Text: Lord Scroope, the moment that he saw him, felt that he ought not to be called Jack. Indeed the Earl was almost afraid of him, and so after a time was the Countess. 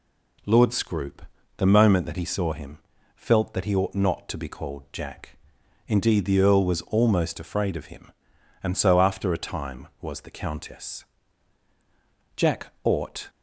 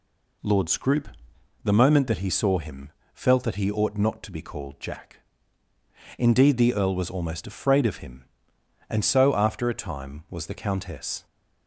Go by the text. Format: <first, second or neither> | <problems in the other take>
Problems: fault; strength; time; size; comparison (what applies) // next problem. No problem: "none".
second | goes on to say "Jack ought"; noticeable; from 12.3 s on; 0.94 s long